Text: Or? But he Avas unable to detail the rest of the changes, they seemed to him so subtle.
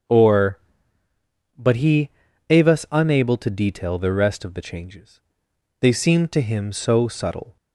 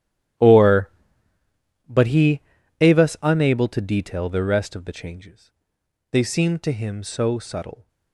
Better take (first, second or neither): first